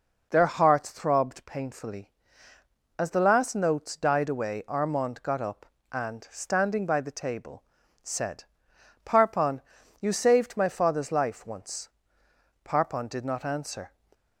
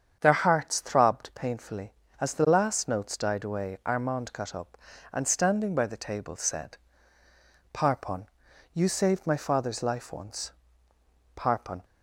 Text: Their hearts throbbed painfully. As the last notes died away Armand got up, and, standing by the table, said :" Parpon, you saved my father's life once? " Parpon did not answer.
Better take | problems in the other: first | starts louder than the rest; strong; until 1.2 s; 8 dB // stops before "did not answer"; at 11.8 s

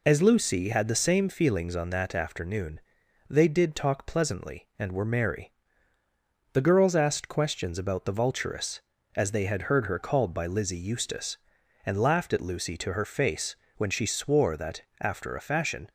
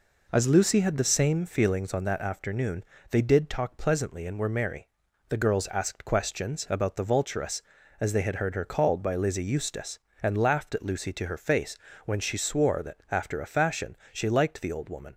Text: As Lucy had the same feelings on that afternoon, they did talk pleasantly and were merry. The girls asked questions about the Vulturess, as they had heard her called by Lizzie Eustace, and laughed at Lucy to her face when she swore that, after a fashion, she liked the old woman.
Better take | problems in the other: second | pauses between "face" and "when"; slight; at 13.5 s; 0.20 s long; slight in the second // stops before "she liked the old woman"; at 15.8 s

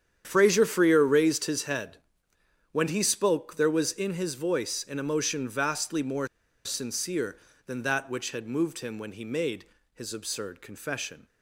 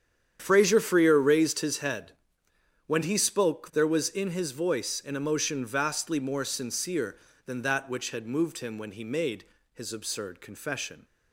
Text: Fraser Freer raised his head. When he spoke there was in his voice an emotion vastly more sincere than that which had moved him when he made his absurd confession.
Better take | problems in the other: second | starts louder than the rest; strong; until 1.2 s; 8.5 dB; strong in the second // pauses between "more" and "sincere"; at 6.2 s; 0.39 s long // pauses between "made" and "his"; slight; at 9.6 s; 0.28 s long; slight in the second

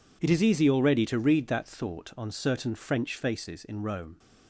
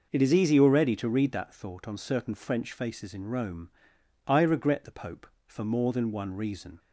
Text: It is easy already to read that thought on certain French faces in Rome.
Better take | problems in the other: first | goes on to say "I regret the Pope for more than one reason"; strong; from 4.2 s on; 2.5 s long

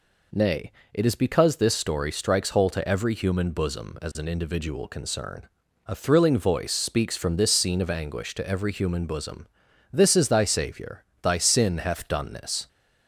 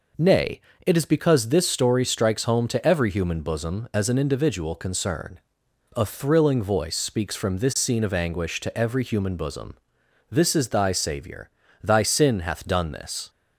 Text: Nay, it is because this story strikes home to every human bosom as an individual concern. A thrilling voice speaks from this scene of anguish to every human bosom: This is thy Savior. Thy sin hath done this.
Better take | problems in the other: second | says "hole" for "home"; at 2.5 s

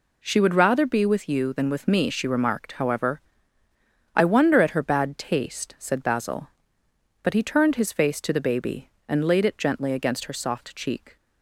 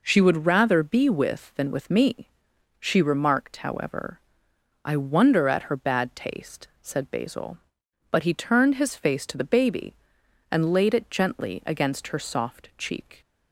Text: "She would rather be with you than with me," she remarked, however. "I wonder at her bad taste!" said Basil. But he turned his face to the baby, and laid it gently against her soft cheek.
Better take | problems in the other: first | skips "you"; at 1.5 s

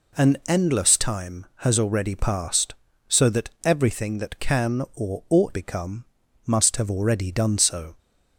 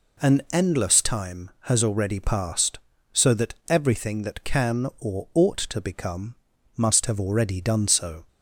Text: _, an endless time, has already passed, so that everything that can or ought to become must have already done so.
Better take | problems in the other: second | skips "to"; at 5.5 s // pauses between "become" and "must"; at 6.0 s; 0.42 s long; also in the second

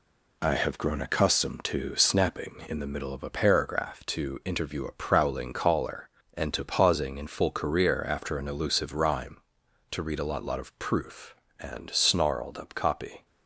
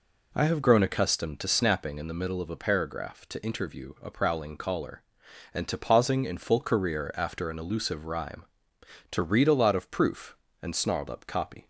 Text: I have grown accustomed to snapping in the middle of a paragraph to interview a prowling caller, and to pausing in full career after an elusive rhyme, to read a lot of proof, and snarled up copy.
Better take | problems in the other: second | says "lot" twice; at 10.4 s

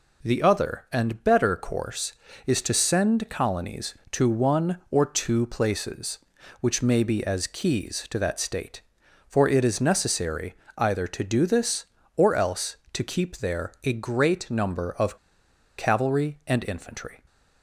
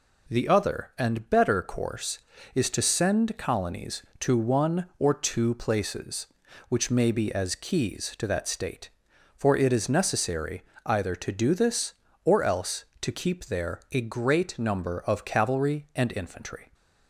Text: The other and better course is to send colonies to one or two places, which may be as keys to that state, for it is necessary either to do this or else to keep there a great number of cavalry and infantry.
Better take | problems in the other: second | pauses between "necessary" and "either"; slight; at 10.5 s; 0.24 s long; slight in the second // pauses between "of" and "cavalry"; noticeable; at 15.1 s; 0.62 s long

